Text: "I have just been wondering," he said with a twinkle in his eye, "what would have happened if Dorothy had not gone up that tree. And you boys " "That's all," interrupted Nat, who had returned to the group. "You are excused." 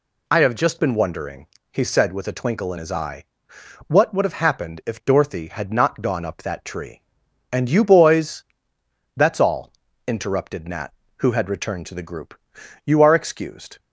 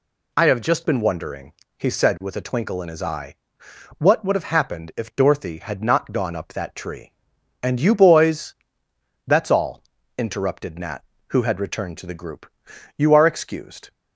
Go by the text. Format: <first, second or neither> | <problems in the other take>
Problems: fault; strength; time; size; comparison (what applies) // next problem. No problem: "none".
neither | none